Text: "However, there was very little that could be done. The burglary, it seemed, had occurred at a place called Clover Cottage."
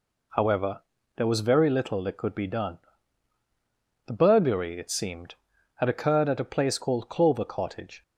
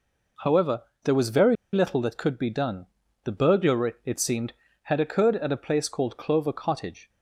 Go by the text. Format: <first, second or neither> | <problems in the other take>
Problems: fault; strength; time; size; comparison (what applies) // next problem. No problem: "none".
first | pauses between "very" and "little"; slight; at 1.5 s; 0.17 s long